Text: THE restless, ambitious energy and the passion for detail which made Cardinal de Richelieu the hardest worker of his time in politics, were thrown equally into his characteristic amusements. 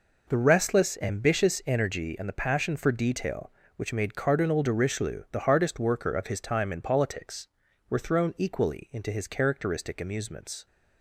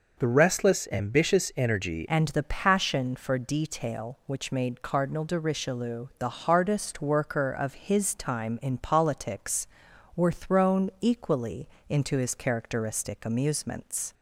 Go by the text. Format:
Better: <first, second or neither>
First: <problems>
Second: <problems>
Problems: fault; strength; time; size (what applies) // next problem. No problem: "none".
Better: first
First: none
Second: changes voice at "and"; from 2.0 s on; 12.1 s long // pauses between "equally" and "into"; slight; at 11.6 s; 0.22 s long